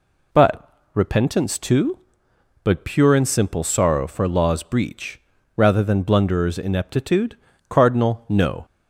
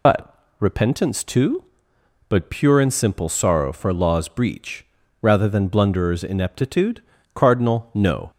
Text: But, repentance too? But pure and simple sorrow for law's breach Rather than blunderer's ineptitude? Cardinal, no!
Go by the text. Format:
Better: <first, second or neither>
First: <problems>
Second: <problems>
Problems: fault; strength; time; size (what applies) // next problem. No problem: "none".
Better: first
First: pauses between "breach" and "Rather"; at 5.1 s; 0.38 s long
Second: loses the start of "But"; at 0.0 s; 70 ms // pauses between "breach" and "Rather"; at 4.8 s; 0.38 s long